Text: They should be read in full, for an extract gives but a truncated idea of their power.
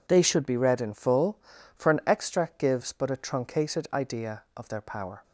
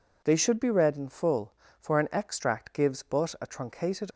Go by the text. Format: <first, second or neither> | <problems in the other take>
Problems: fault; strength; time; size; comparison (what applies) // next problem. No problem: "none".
first | stops before "idea of their power"; at 4.1 s